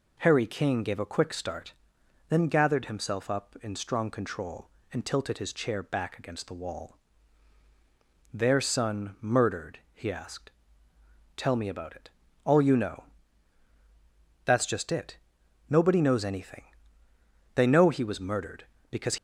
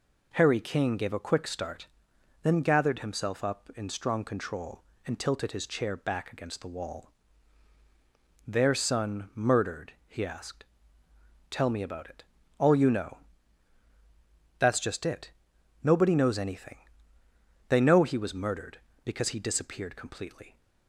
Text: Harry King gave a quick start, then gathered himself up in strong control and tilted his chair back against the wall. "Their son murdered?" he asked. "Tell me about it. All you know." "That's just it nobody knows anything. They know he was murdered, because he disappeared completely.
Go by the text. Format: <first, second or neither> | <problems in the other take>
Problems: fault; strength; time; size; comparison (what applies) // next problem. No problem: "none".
second | pauses between "it" and "nobody"; noticeable; at 15.1 s; 0.50 s long; noticeable in the second // stops before "he disappeared completely"; at 19.1 s